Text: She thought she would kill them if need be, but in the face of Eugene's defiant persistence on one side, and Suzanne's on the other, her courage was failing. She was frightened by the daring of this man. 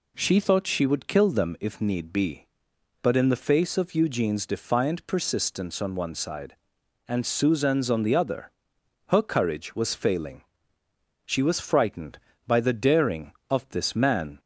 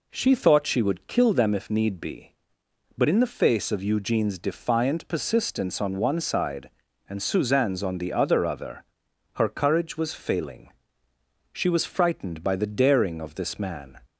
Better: first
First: none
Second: says "other" twice; at 8.4 s

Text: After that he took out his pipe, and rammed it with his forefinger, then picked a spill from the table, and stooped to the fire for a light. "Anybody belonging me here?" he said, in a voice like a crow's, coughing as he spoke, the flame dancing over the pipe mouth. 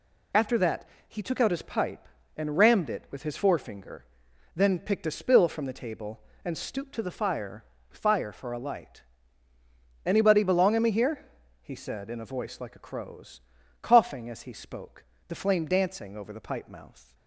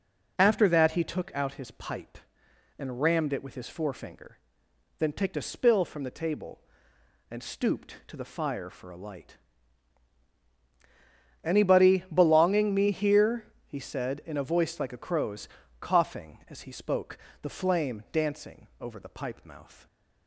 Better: second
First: pauses between "that" and "he"; slight; at 0.8 s; 0.22 s long // says "fire" twice; at 7.8 s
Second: none

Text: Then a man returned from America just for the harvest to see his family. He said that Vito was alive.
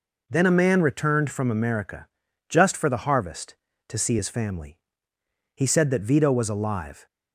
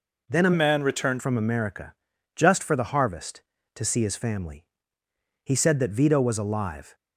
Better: first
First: pauses between "America" and "just"; at 2.0 s; 0.42 s long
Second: changes voice from "man" to "returned"; from 0.5 to 1.2 s; 0.7 s long // pauses between "America" and "just"; at 1.9 s; 0.42 s long

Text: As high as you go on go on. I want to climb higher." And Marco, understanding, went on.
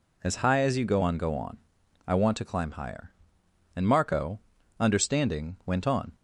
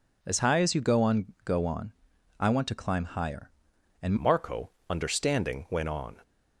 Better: first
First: none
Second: changes voice at "Marco"; from 4.1 s on; 2.0 s long

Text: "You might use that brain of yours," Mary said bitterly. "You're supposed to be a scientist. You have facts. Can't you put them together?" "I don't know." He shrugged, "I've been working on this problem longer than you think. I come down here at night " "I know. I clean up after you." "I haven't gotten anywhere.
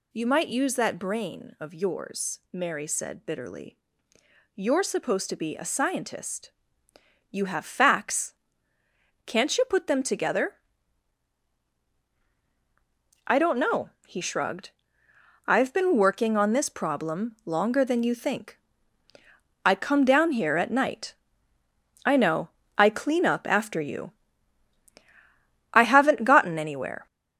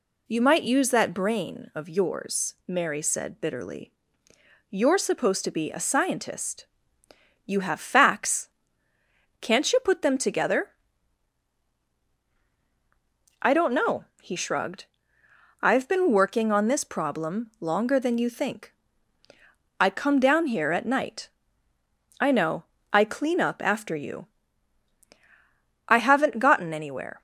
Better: second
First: gets louder; noticeable; throughout; 4 dB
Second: none

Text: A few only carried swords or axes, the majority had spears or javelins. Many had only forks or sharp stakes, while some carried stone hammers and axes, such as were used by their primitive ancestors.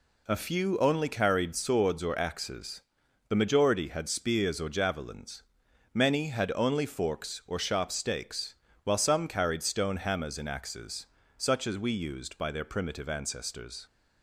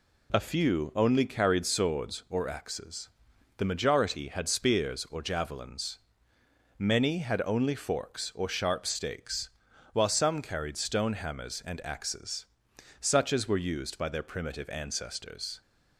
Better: second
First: says "we" for "were"; at 11.7 s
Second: none

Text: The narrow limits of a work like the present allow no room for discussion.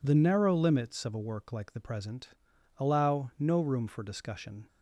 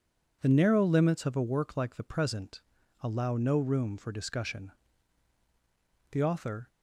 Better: first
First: pauses between "present" and "allow"; noticeable; at 2.2 s; 0.48 s long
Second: pauses between "present" and "allow"; at 2.6 s; 0.40 s long // goes on to say "The author"; from 6.1 s on; 0.56 s long

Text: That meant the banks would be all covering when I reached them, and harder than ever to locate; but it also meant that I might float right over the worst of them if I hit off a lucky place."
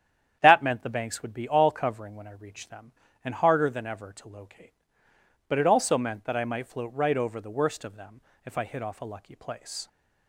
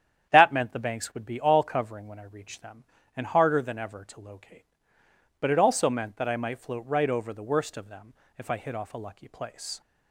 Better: neither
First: starts louder than the rest; strong; until 1.4 s; 9.5 dB // pauses between "them" and "if"; slight; at 8.1 s; 0.24 s long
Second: starts louder than the rest; strong; until 1.3 s; 9.5 dB // pauses between "them" and "if"; slight; at 8.1 s; 0.24 s long

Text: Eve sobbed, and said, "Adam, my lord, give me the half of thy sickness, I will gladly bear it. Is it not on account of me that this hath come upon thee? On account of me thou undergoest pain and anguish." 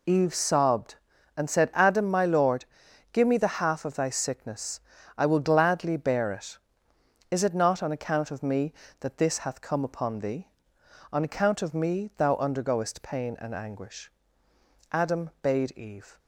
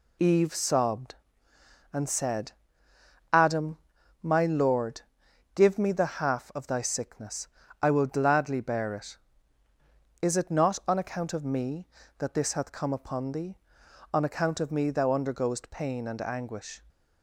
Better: second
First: goes on to say "Adam bade Eve"; noticeable; from 14.9 s on; 1.2 s long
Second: none

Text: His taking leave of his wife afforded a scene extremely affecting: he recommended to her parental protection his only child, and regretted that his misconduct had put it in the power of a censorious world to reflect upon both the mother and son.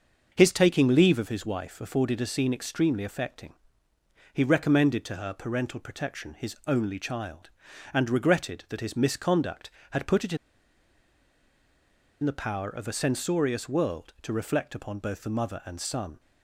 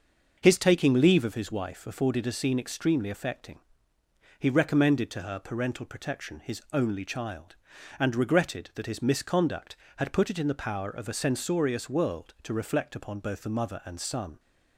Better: second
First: starts louder than the rest; until 1.3 s; 6.5 dB // pauses between "in" and "the"; strong; at 10.3 s; 1.8 s long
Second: starts louder than the rest; until 1.4 s; 6.5 dB

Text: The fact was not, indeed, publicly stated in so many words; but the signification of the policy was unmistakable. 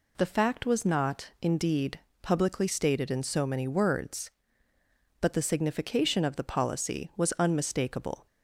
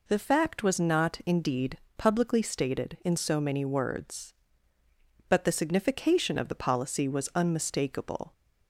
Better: neither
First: none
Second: none

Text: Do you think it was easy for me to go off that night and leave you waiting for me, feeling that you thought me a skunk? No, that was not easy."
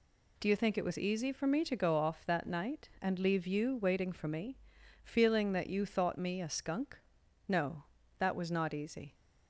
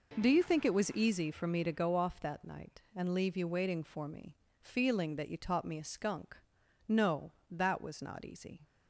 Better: first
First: none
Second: says "taught" for "thought"; at 5.3 s

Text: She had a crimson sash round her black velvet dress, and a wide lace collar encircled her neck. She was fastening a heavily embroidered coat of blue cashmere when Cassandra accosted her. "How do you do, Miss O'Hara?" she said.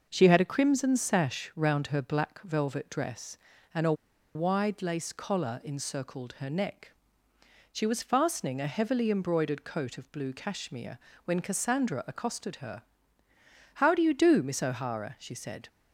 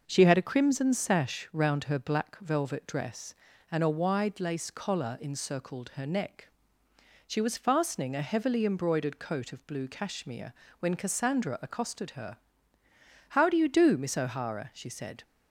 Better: second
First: pauses between "a" and "wide"; at 3.9 s; 0.42 s long // pauses between "cashmere" and "when"; slight; at 10.9 s; 0.28 s long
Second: pauses between "cashmere" and "when"; slight; at 10.5 s; 0.28 s long

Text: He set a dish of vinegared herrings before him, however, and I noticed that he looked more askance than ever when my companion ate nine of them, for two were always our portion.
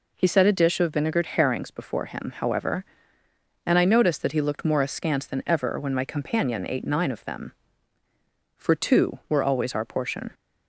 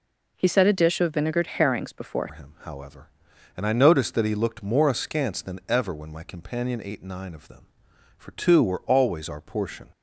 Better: first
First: none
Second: changes voice at "him"; from 2.3 s on; 7.6 s long

